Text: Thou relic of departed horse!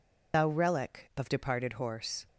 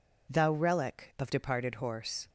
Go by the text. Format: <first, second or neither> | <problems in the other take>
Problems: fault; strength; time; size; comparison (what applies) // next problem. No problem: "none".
second | loses the start of "Thou"; at 0.3 s; 90 ms